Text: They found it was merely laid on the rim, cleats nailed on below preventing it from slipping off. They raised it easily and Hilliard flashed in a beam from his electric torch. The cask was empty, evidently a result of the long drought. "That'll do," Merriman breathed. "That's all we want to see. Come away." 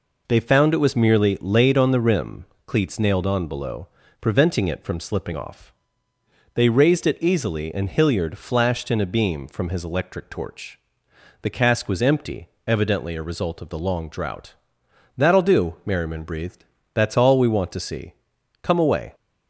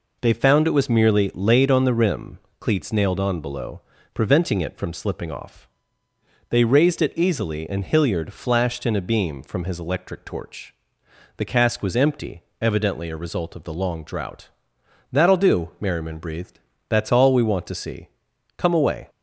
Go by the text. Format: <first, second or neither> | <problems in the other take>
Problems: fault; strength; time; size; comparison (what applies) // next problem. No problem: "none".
neither | pauses between "below" and "preventing"; slight; the same in both